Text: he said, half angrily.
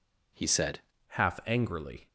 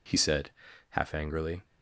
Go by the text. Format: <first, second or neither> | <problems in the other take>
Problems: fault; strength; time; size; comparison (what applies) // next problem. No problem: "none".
second | changes voice at "half"; from 1.0 s on; 1.0 s long